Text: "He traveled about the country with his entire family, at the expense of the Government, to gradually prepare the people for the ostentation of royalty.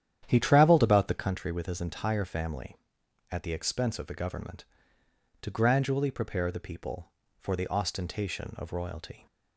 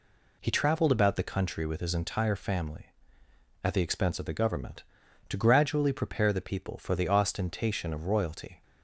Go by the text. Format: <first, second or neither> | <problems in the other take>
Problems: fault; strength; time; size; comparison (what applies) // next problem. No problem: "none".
second | starts louder than the rest; strong; until 1.3 s; 10 dB